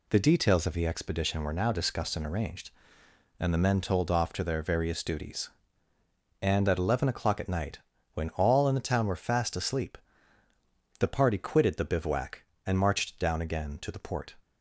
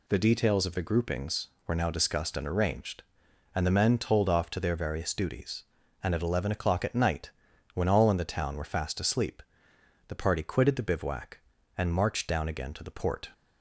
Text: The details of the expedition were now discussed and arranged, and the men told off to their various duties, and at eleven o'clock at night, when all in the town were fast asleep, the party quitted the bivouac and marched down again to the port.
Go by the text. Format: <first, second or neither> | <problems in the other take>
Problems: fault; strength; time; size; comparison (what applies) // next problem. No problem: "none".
first | says "groupings" for "expedition"; at 0.8 s